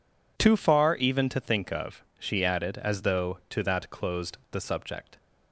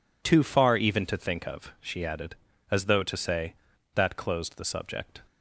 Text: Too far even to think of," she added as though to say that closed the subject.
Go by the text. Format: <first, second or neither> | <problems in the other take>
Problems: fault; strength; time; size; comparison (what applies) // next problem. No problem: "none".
second | skips "say"; at 3.6 s